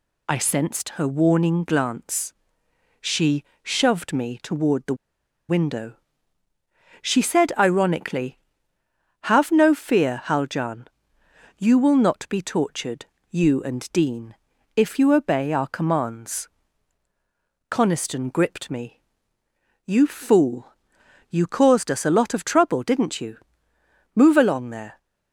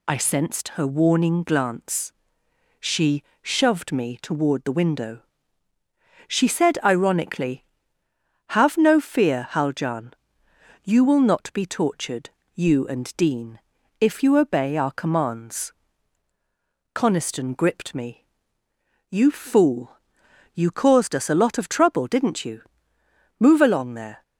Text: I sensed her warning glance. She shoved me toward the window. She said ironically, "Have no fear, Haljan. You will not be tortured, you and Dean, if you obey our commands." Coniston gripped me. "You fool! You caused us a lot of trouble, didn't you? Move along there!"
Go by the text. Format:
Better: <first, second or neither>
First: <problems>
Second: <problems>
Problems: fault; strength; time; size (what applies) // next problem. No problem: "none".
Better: second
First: pauses between "She" and "shoved"; slight; at 3.4 s; 0.20 s long // pauses between "the" and "window"; noticeable; at 4.9 s; 0.52 s long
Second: pauses between "She" and "shoved"; slight; at 3.2 s; 0.20 s long